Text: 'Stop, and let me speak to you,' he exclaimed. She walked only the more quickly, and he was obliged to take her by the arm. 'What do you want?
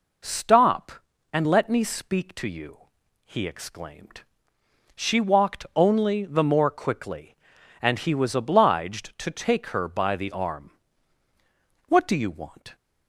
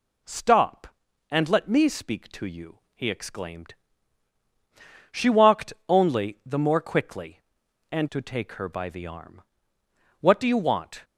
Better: first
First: none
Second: pauses between "walked" and "only"; slight; at 5.7 s; 0.16 s long // skips "he was obliged"; at 8.1 s

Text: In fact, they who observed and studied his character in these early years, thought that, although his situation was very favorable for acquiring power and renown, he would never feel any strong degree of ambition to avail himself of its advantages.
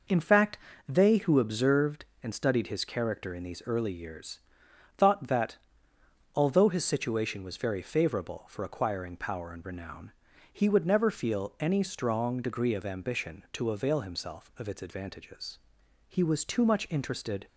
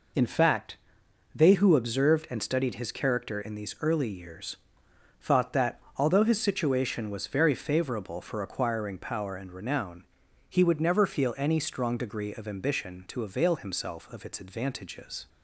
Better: second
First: goes on to say "He was too much interested"; from 16.0 s on; 1.3 s long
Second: none

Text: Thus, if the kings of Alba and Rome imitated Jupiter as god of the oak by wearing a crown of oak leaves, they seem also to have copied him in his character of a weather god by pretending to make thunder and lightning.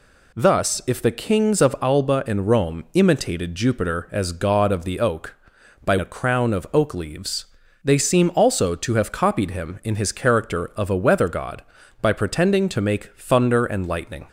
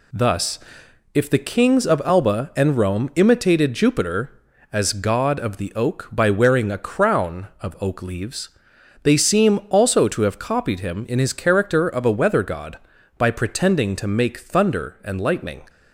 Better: second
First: skips "wearing"; at 5.9 s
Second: none

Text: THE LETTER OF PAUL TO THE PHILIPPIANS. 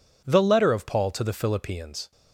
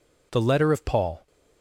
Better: first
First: none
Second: stops before "TO THE PHILIPPIANS"; at 1.2 s

